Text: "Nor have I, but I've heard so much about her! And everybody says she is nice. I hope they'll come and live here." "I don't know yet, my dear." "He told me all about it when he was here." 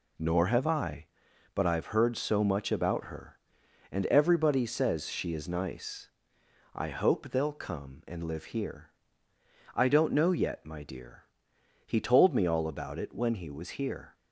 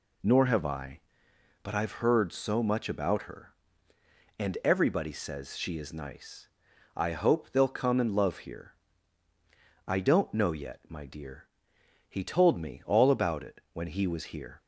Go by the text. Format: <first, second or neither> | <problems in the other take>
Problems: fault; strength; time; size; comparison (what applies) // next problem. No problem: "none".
first | says "love" for "live"; at 8.1 s